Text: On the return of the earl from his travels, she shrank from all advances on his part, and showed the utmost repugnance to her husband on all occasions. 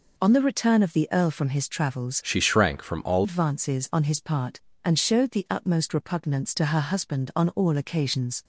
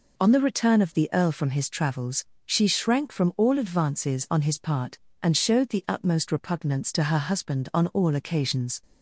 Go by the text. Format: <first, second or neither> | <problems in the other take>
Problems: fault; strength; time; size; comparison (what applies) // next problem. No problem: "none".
second | changes voice from "she" to "all"; from 2.2 to 3.2 s; 1.0 s long